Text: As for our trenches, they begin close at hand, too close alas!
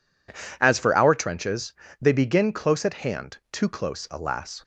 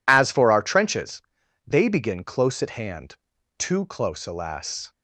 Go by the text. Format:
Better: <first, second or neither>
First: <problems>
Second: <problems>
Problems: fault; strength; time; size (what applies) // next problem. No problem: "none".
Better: neither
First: none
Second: none